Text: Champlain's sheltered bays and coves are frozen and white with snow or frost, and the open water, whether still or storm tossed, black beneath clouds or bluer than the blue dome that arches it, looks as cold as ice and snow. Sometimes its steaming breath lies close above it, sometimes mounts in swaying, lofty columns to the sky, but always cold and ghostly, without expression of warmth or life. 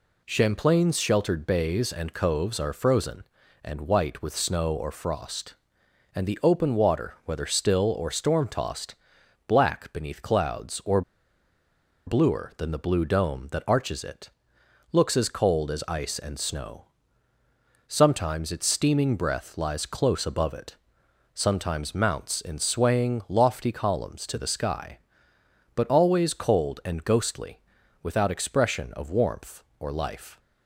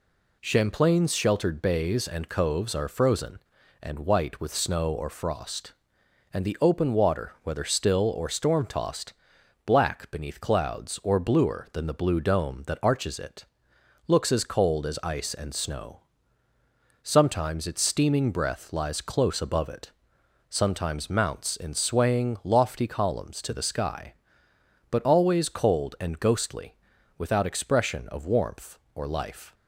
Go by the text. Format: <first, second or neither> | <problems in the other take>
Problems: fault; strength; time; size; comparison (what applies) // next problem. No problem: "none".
second | pauses between "or" and "bluer"; at 11.0 s; 1.0 s long